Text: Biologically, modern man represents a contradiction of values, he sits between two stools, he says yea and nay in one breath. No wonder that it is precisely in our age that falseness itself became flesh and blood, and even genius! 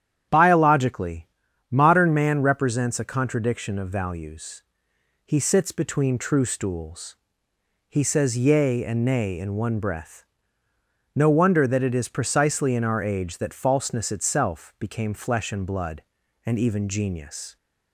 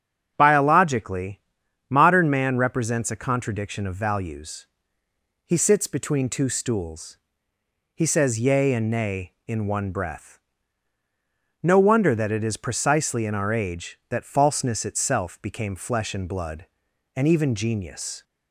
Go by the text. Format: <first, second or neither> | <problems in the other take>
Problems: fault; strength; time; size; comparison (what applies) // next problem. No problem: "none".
second | starts louder than the rest; strong; until 1.7 s; 9.5 dB; strong in the second // says "true" for "two"; at 6.1 s